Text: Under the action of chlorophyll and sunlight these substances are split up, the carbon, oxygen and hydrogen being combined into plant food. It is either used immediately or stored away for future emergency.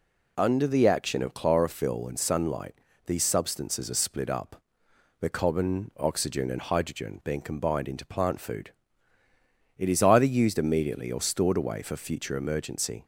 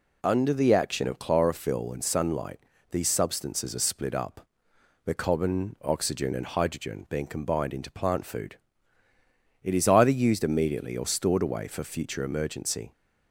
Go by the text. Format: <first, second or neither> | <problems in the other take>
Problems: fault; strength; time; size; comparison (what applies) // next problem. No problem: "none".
neither | pauses between "sunlight" and "these"; slight; the same in both